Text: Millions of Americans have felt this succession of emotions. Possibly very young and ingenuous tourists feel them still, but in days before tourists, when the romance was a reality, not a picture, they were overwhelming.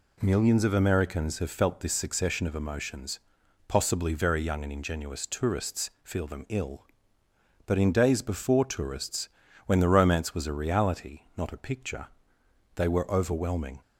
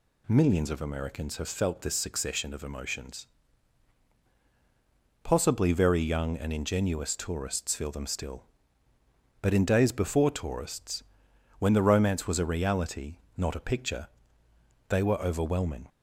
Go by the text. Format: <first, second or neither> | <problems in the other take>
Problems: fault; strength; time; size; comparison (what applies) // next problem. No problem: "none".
second | says "ill" for "still"; at 6.4 s